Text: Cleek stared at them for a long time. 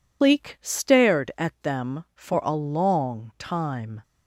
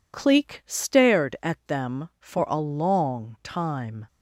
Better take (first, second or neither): second